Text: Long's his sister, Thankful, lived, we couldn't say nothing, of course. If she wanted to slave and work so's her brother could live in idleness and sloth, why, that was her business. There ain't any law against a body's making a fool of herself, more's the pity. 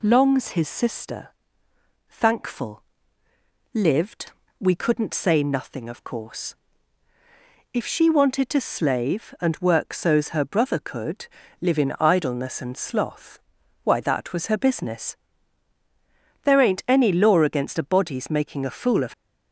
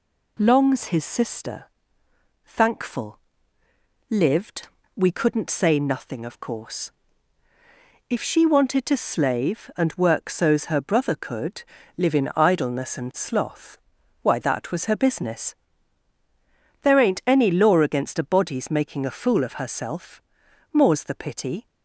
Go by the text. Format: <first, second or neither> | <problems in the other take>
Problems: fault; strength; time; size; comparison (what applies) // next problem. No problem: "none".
second | pauses between "could" and "live"; slight; at 11.2 s; 0.32 s long; slight in the second // stops before "herself more's the pity"; at 19.1 s